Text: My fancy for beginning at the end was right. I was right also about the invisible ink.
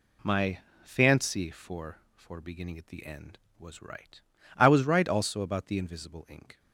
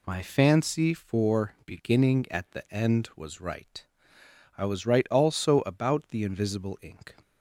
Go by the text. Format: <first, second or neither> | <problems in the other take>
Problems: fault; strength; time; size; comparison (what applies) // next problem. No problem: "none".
second | pauses between "My" and "fancy"; slight; at 0.5 s; 0.24 s long // says "for" twice; at 2.1 s